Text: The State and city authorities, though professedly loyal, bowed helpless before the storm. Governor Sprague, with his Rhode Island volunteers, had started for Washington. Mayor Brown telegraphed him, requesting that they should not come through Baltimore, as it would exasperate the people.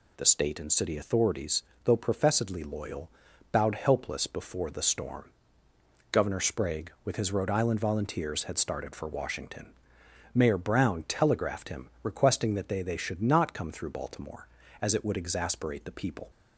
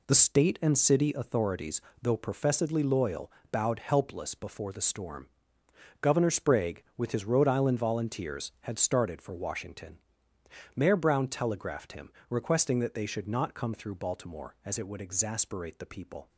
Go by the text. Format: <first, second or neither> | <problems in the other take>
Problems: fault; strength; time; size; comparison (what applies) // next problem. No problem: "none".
second | says "they" twice; at 12.8 s